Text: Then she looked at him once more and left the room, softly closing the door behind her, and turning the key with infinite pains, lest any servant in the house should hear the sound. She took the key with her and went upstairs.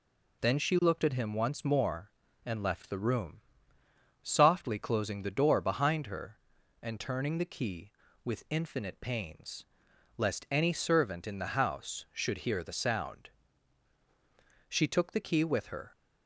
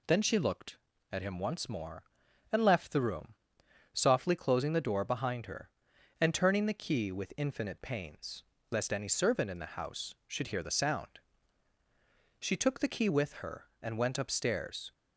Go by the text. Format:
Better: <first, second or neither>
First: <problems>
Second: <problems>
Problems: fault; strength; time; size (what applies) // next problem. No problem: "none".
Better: second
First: stops before "and went upstairs"; at 15.9 s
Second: none